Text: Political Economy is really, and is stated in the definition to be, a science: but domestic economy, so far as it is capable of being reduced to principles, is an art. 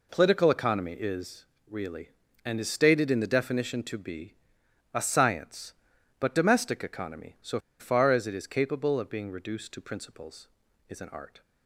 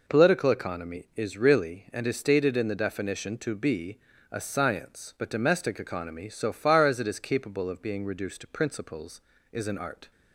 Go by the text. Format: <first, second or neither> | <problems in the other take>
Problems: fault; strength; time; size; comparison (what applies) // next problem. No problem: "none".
second | pauses between "is" and "really"; slight; at 1.4 s; 0.26 s long // pauses between "so" and "far"; slight; at 7.5 s; 0.19 s long